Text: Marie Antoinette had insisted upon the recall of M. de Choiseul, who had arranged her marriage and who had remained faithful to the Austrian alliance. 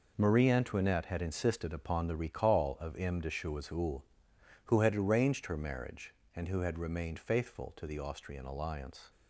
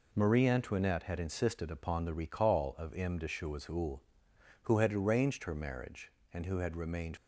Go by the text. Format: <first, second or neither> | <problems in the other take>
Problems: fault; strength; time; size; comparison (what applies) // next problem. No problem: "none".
first | stops before "faithful to the Austrian alliance"; at 7.1 s